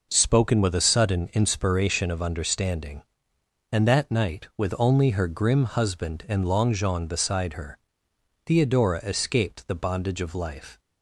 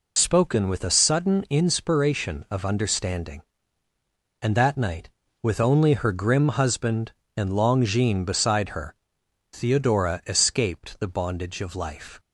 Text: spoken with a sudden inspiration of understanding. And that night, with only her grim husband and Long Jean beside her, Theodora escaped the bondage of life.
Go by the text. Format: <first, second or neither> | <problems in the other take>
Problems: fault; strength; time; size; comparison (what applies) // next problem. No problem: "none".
first | loses the start of "spoken"; at 0.1 s; 45 ms